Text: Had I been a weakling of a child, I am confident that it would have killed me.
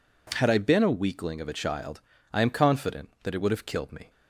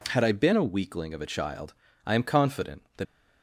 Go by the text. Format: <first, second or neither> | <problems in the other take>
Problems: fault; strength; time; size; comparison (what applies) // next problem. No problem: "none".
first | stops before "it would have killed me"; at 3.0 s